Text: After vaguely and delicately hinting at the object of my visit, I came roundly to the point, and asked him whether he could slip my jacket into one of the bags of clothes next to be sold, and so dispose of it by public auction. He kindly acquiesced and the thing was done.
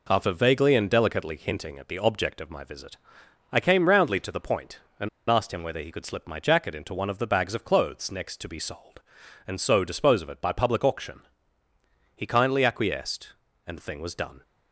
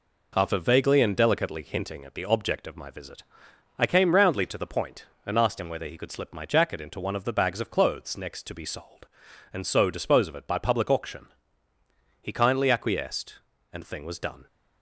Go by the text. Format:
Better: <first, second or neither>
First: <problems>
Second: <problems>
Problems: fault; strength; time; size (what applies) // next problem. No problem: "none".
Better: second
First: pauses between "and" and "asked"; slight; at 5.0 s; 0.20 s long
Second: none